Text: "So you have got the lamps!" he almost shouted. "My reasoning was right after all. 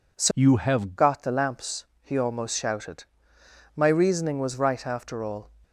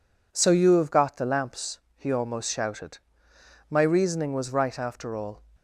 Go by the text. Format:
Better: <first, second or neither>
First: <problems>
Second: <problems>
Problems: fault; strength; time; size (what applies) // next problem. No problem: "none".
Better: second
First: changes voice from "you" to "have"; from 0.3 to 0.9 s; 0.6 s long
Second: none